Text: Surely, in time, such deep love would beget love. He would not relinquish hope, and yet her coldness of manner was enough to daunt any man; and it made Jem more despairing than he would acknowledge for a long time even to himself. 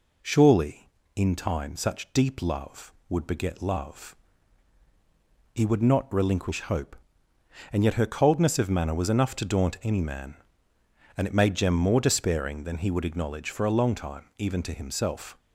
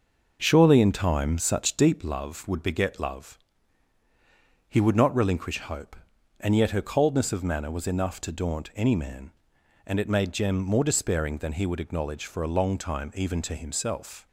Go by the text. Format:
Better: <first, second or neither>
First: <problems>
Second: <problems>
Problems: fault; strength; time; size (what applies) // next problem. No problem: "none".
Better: first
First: none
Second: starts louder than the rest; noticeable; until 2.1 s; 6 dB